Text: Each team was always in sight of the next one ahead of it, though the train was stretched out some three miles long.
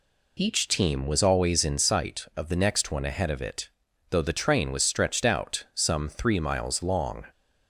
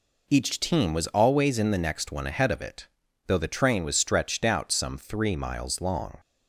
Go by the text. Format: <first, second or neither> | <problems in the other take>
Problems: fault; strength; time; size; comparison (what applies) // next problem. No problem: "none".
first | skips "sight of"; at 1.7 s